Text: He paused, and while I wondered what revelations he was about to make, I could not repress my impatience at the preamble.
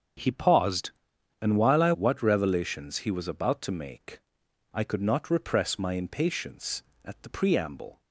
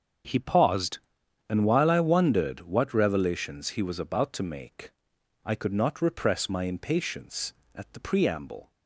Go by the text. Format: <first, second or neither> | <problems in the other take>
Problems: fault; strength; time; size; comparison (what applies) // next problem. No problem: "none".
second | starts louder than the rest; until 1.6 s; 7 dB; also in the second // skips "wondered"; at 1.9 s